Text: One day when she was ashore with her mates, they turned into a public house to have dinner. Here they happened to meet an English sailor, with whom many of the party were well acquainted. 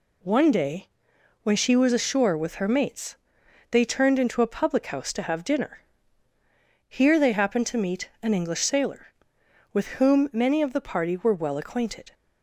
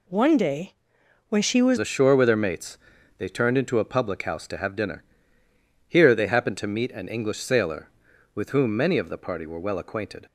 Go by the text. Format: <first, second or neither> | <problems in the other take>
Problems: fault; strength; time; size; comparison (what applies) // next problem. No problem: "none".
first | pauses between "day" and "when"; noticeable; at 0.7 s; 0.58 s long; noticeable in the first // changes voice at "ashore"; from 1.7 s on; 8.5 s long